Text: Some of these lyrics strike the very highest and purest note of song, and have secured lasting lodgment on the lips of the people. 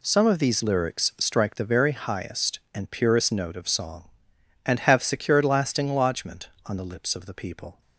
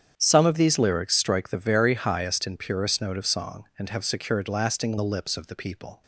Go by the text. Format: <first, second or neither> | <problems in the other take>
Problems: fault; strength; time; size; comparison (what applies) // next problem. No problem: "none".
first | starts louder than the rest; strong; until 1.1 s; 8.5 dB // skips "lodgment on"; at 4.9 s